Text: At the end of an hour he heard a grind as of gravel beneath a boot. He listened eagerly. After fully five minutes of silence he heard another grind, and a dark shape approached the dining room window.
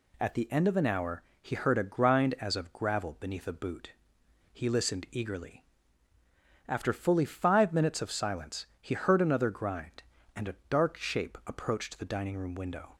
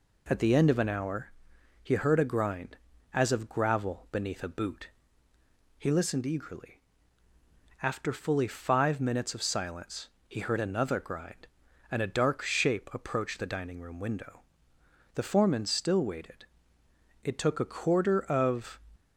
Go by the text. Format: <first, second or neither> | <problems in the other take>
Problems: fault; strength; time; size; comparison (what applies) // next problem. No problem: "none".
first | pauses between "hour" and "he"; noticeable; at 1.3 s; 0.52 s long; slight in the first // pauses between "silence" and "he"; slight; at 10.0 s; 0.18 s long; slight in the first // goes on to say "The foreman still waited It took a quarter of"; strong; from 15.1 s on; 3.6 s long